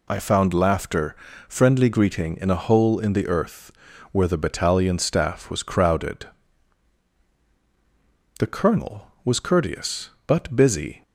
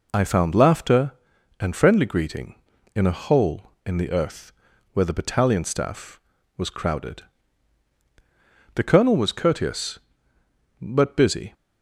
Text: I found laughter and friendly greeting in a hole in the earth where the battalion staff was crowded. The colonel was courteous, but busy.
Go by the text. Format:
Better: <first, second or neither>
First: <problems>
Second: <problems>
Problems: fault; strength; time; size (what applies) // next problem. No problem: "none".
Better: second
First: skips "and"; at 1.3 s // pauses between "earth" and "where"; at 3.7 s; 0.40 s long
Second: pauses between "earth" and "where"; at 4.5 s; 0.40 s long